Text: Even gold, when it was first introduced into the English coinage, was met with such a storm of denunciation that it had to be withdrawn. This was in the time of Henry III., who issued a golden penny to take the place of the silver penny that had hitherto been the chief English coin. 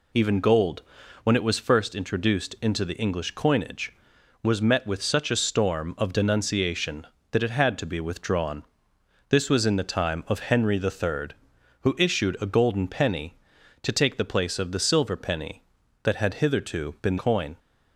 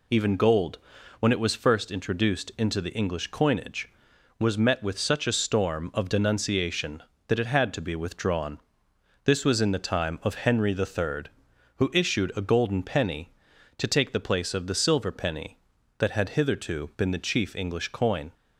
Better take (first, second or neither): second